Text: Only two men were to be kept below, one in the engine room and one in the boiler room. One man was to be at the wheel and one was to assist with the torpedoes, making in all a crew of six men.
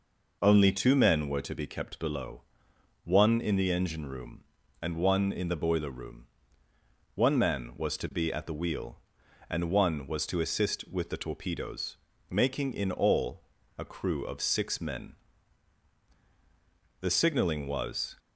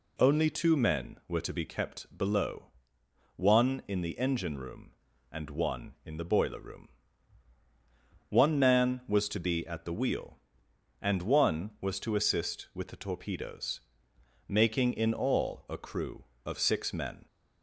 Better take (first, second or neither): second